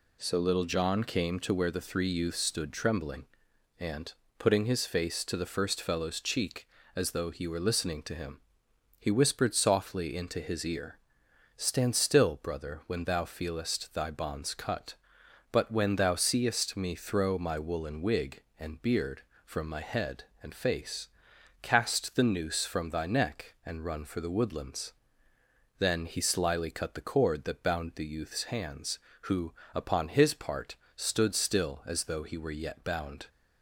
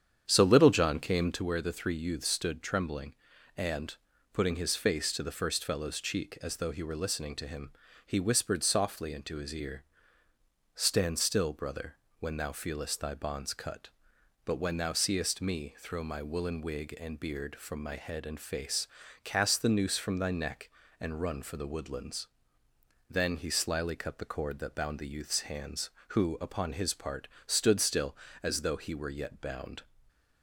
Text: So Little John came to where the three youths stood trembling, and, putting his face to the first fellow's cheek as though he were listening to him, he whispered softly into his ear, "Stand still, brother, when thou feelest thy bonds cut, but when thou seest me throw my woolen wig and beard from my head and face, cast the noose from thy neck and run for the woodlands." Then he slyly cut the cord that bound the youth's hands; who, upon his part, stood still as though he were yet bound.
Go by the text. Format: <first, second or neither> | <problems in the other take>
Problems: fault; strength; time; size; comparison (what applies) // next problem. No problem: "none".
first | starts louder than the rest; strong; until 1.4 s; 8.5 dB // stays silent after the last word; slight; from 29.8 s on; 0.6 s long